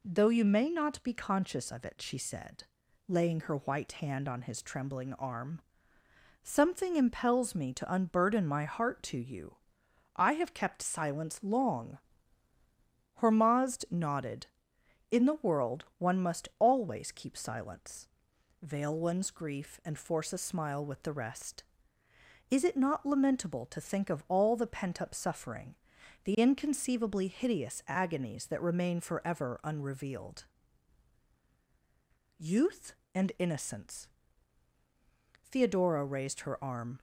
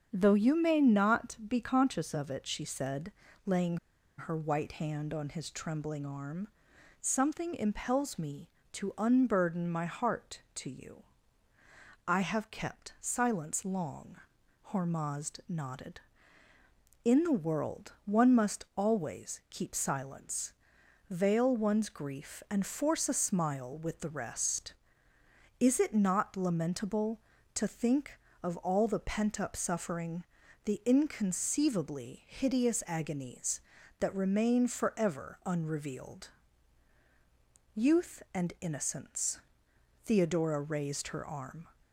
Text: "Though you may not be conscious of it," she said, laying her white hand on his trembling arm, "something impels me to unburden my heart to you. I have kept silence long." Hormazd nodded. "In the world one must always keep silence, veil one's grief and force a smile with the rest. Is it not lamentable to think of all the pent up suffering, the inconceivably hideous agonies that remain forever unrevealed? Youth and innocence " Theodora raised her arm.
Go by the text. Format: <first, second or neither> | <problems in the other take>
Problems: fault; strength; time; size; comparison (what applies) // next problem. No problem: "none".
first | starts louder than the rest; until 1.1 s; 7 dB // pauses between "laying" and "her"; at 3.7 s; 0.42 s long